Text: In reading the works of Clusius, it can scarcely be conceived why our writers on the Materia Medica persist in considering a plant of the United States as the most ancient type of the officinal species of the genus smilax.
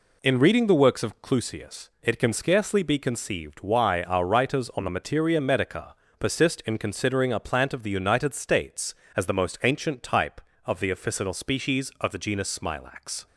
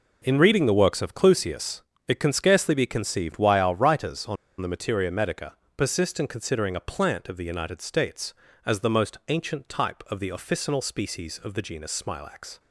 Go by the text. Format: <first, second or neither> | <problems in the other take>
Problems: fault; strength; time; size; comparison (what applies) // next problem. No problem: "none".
first | pauses between "on" and "the"; slight; at 4.3 s; 0.25 s long // pauses between "Medica" and "persist"; slight; at 5.5 s; 0.22 s long; slight in the first